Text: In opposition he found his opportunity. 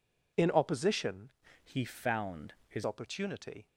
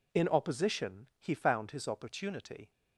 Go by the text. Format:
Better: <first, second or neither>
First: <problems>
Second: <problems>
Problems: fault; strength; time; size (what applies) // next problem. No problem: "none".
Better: second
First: changes voice from "he" to "his"; from 1.6 to 2.8 s; 1.2 s long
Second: none